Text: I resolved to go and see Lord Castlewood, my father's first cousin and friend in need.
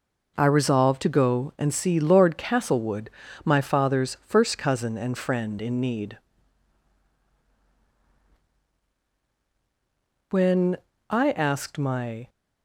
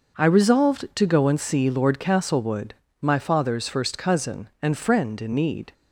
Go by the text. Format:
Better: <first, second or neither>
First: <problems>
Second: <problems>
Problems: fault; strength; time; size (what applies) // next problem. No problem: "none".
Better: second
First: goes on to say "When I asked my"; strong; from 10.3 s on; 1.9 s long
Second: none